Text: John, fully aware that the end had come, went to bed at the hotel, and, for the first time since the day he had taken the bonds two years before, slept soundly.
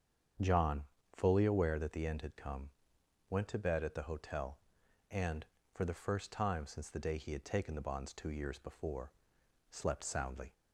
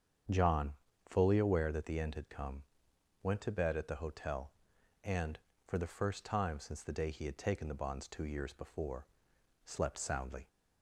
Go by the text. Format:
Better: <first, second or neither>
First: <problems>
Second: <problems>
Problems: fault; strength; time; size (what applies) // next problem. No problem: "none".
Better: neither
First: starts louder than the rest; strong; until 1.7 s; 7.5 dB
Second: starts louder than the rest; strong; until 1.6 s; 7.5 dB